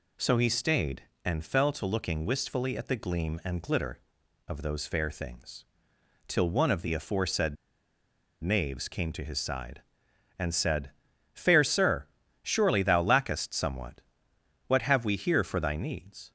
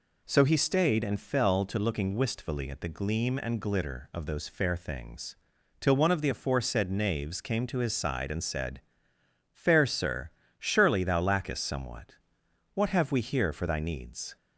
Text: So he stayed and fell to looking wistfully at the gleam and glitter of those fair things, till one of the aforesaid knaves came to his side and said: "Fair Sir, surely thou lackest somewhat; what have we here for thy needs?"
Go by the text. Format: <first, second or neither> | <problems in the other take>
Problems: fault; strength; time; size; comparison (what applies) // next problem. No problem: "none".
second | pauses between "aforesaid" and "knaves"; noticeable; at 7.5 s; 0.87 s long